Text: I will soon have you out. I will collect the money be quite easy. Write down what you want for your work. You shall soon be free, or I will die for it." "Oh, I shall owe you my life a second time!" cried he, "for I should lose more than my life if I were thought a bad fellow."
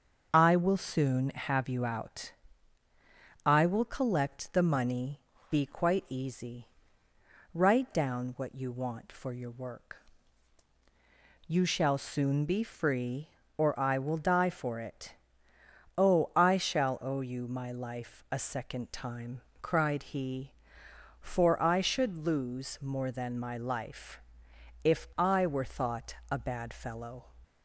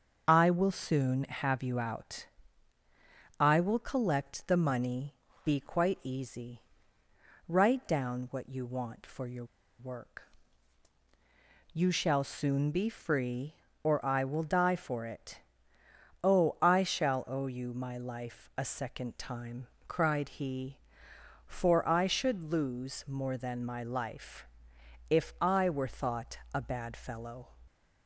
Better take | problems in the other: first | starts louder than the rest; until 1.2 s; 6.5 dB; also in the first // pauses between "money" and "be"; slight; at 5.1 s; 0.30 s long; slight in the first // pauses between "your" and "work"; slight; at 9.4 s; 0.34 s long // pauses between "life" and "if"; noticeable; at 24.4 s; 0.64 s long; noticeable in the first // pauses between "thought" and "a"; slight; at 26.3 s; 0.16 s long; slight in the first

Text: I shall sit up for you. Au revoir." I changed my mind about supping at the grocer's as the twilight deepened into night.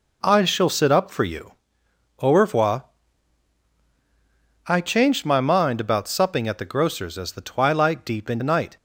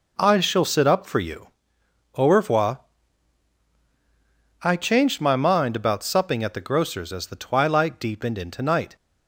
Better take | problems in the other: second | skips "into"; at 8.4 s

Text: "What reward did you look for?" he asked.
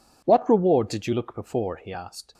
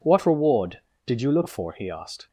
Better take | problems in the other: second | says "before" for "for"; at 1.3 s

